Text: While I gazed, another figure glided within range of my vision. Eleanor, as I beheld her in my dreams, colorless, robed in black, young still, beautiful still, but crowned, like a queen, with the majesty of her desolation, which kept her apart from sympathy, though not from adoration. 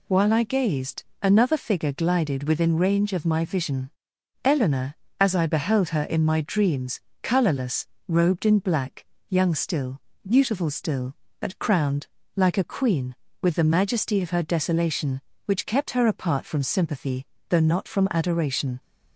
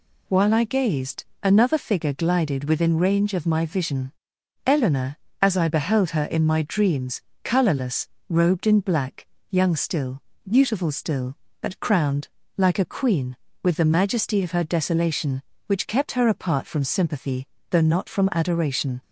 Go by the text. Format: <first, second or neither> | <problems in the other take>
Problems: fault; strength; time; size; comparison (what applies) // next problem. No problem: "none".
neither | none